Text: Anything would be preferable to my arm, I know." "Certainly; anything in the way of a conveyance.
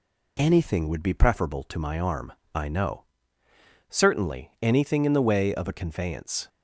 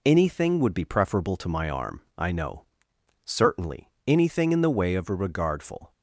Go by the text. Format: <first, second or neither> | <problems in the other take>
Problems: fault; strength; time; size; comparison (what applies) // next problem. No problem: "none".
first | says "regardful" for "conveyance"; at 5.1 s